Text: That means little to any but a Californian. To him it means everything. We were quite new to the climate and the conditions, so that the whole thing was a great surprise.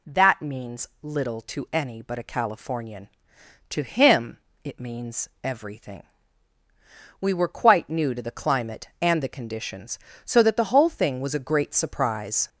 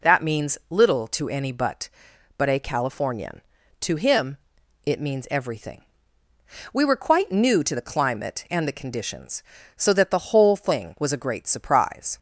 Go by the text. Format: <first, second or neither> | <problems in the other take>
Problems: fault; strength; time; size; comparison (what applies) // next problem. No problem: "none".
first | says "but" twice; at 2.3 s // pauses between "him" and "it"; noticeable; at 4.3 s; 0.48 s long; slight in the first